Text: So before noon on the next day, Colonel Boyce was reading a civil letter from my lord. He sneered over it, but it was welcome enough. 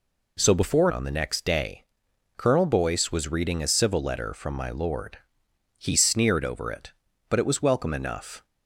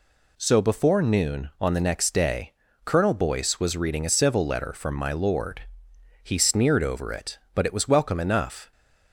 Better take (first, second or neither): second